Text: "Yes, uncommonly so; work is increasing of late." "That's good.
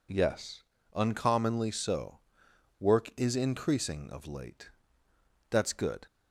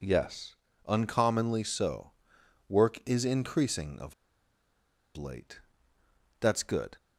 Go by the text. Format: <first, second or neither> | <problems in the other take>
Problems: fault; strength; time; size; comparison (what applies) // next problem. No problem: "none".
first | pauses between "of" and "late"; at 4.1 s; 1.0 s long